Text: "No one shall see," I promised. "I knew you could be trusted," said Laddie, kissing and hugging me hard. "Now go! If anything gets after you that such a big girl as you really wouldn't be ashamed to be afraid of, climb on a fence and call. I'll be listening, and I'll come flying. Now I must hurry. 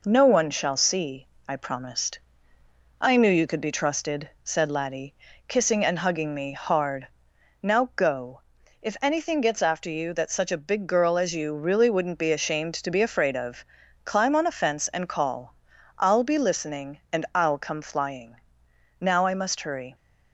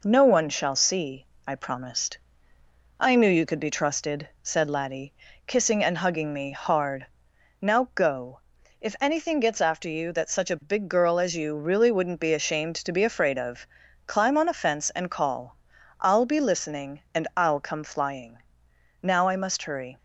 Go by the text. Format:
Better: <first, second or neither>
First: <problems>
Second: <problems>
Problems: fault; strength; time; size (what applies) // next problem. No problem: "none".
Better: neither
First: none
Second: none